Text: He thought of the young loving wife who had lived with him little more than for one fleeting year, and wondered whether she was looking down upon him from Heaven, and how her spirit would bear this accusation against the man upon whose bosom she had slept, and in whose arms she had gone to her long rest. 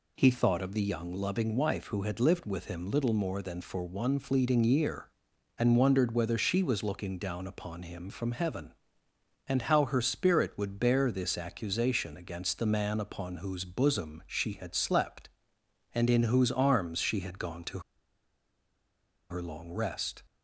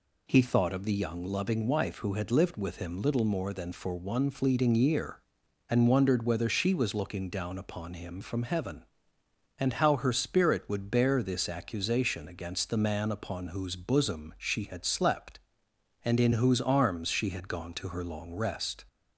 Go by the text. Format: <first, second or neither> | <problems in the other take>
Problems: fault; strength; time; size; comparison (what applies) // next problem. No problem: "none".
second | pauses between "to" and "her"; strong; at 17.7 s; 1.5 s long